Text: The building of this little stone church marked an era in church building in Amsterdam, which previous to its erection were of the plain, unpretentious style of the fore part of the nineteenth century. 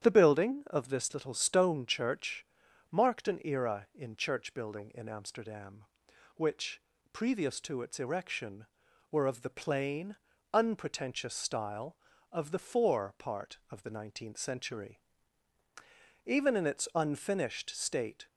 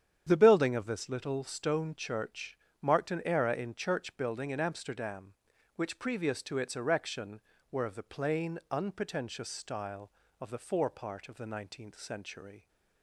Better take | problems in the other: second | starts louder than the rest; strong; until 1.0 s; 9 dB; strong in the second // pauses between "church" and "marked"; noticeable; at 2.4 s; 0.46 s long; slight in the second // pauses between "which" and "previous"; slight; at 6.8 s; 0.32 s long // goes on to say "Even in its unfinished state"; strong; from 16.2 s on; 2.0 s long

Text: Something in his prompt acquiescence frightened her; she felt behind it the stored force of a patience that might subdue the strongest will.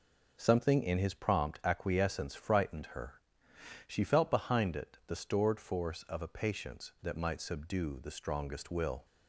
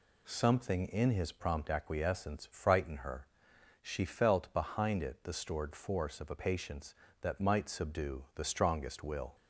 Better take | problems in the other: neither | none

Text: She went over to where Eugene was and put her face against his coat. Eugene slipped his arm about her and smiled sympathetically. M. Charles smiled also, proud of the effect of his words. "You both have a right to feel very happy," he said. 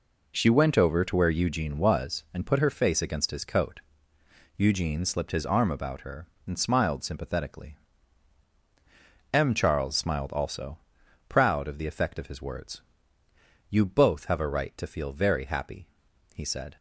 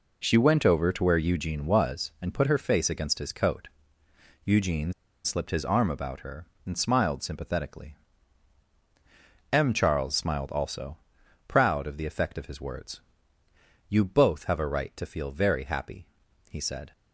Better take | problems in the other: first | pauses between "Eugene" and "slipped"; slight; at 4.9 s; 0.32 s long

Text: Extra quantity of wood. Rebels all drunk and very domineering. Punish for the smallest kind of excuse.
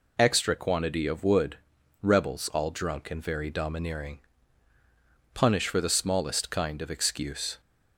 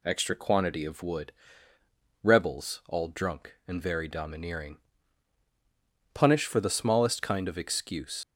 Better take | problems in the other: first | leaves "excuse" unfinished; at 8.2 s; 75 ms

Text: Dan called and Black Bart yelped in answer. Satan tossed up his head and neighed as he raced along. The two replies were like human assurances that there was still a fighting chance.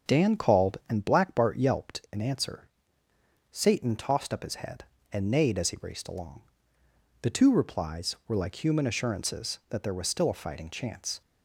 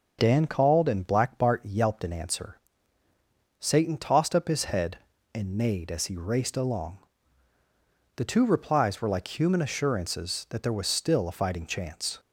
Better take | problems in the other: neither | starts louder than the rest; the same in both

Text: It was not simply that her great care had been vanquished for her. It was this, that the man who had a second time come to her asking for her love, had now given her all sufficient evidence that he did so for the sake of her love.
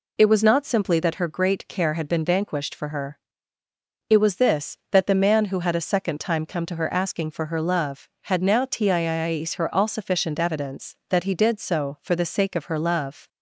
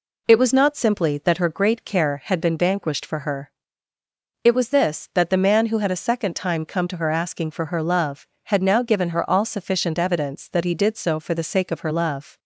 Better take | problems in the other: second | says "tiiis" for "given"; at 8.6 s

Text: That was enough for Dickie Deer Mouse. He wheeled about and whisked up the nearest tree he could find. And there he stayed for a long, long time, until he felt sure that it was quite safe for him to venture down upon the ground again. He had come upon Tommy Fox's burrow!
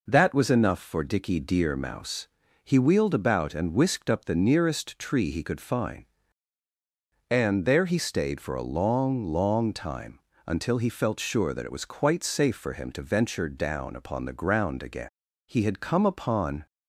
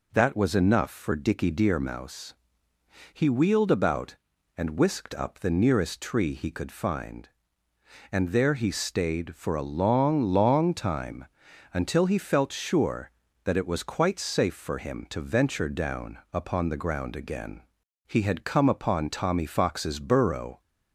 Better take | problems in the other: second | stops before "Tommy Fox's burrow"; at 16.6 s

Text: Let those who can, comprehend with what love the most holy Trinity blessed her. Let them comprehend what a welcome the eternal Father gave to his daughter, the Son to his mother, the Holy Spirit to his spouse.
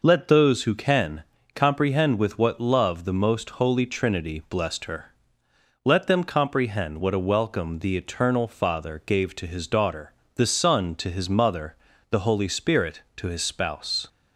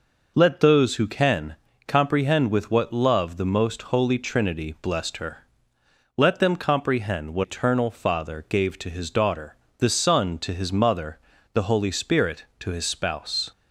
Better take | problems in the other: first | skips "a welcome the"; at 7.4 s

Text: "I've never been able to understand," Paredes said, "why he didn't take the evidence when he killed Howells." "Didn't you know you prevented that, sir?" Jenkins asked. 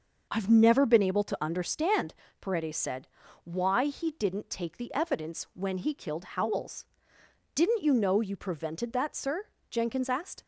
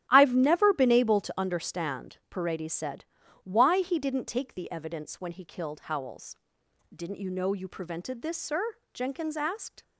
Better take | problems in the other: first | starts louder than the rest; strong; until 1.1 s; 12 dB // says "this" for "that"; at 8.2 s

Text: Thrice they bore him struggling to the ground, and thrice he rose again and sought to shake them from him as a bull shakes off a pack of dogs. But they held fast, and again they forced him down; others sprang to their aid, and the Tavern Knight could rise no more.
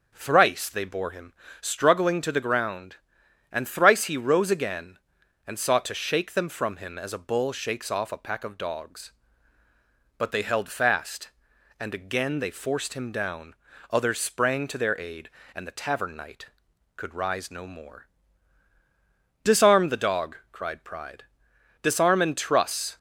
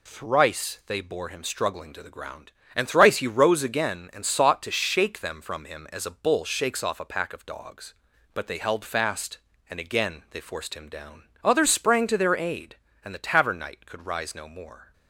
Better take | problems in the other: second | starts louder than the rest; until 1.1 s; 6.5 dB // pauses between "him" and "struggling"; slight; at 1.3 s; 0.26 s long // goes on to say "Disarm the dog cried Pride Disarm and truss"; strong; from 19.4 s on; 3.5 s long

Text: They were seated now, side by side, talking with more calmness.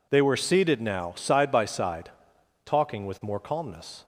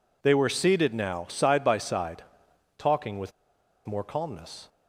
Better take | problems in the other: first | pauses between "with" and "more"; noticeable; at 3.3 s; 0.54 s long

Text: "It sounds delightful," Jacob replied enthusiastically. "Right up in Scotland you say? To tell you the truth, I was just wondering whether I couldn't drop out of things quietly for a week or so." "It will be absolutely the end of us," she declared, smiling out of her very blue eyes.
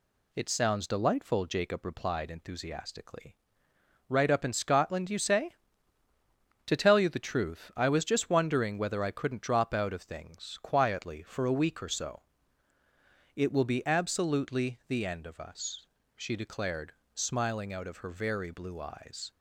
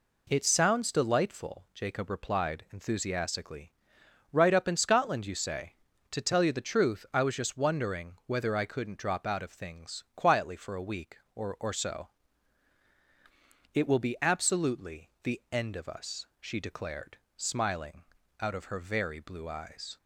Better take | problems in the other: first | says "or" twice; at 11.6 s // pauses between "smiling" and "out"; at 18.0 s; 0.38 s long

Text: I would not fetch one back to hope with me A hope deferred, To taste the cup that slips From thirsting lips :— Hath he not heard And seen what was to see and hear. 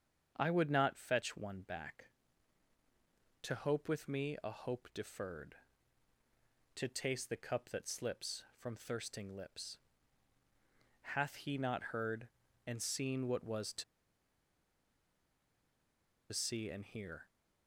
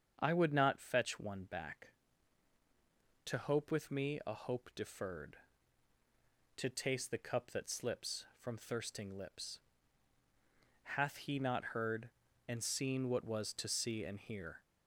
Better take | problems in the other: second | starts louder than the rest; strong; until 1.3 s; 7.5 dB; strong in the second // pauses between "to" and "see"; strong; at 13.8 s; 2.4 s long

